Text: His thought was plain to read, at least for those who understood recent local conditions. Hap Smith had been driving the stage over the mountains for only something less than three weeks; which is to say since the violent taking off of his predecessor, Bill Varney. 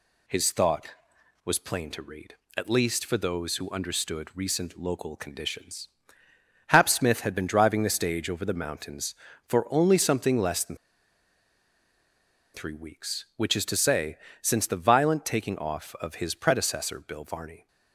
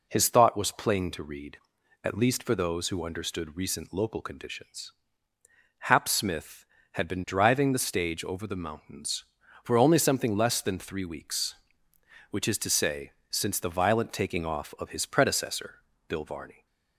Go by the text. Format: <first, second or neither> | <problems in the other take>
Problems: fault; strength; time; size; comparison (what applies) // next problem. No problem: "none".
second | pauses between "than" and "three"; strong; at 10.7 s; 1.7 s long // pauses between "say" and "since"; slight; at 14.1 s; 0.24 s long; slight in the second